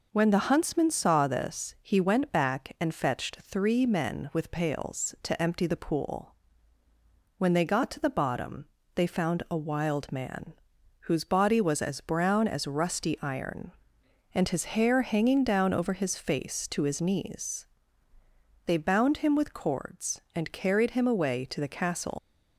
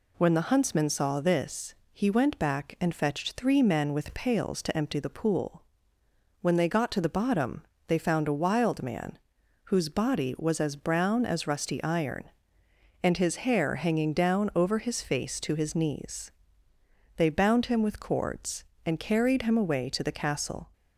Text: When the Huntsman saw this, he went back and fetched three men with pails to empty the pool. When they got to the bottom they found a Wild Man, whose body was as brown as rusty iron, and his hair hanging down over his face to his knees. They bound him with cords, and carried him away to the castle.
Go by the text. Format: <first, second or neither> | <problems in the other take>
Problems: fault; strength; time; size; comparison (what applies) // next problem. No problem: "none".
second | pauses between "bottom" and "they"; slight; at 8.6 s; 0.30 s long; slight in the second // leaves "castle" unfinished; at 22.1 s; 125 ms